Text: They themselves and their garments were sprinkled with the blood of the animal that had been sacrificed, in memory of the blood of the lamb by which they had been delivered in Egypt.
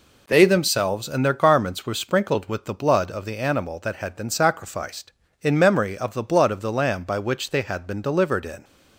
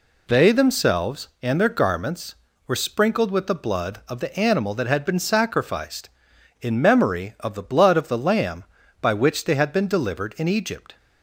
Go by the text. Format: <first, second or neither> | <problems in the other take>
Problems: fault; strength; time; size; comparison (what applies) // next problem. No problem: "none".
second | stops before "Egypt"; at 8.6 s